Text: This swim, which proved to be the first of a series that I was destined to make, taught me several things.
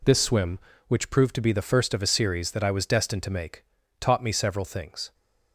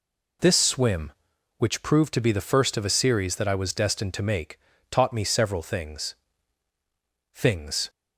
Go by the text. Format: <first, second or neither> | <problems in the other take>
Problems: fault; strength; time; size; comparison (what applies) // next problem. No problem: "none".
first | says "things" twice; at 7.3 s